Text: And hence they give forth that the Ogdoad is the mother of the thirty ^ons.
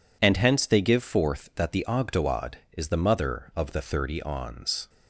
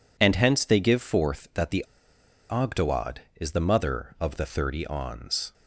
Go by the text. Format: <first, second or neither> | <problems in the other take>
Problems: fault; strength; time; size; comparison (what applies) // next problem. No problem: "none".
first | pauses between "the" and "Ogdoad"; noticeable; at 1.8 s; 0.64 s long